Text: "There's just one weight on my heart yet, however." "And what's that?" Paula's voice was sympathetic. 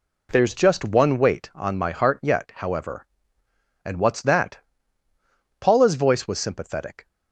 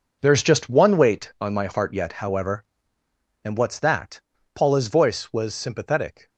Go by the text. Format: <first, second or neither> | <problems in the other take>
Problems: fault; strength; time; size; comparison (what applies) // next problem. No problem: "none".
first | gets quieter; strong; throughout; 12 dB